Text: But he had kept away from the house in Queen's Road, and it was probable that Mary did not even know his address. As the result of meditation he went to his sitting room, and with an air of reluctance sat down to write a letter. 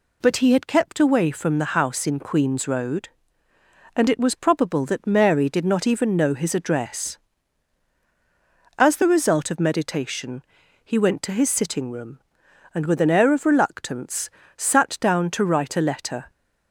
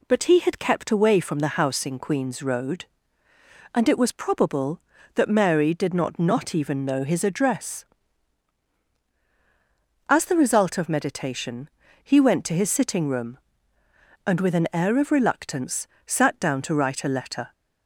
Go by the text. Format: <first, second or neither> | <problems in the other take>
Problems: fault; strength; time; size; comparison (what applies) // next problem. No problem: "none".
first | says "not" twice; at 6.1 s // pauses between "meditation" and "he"; slight; at 11.6 s; 0.34 s long; also in the first // pauses between "reluctance" and "sat"; slight; at 15.8 s; 0.18 s long; slight in the first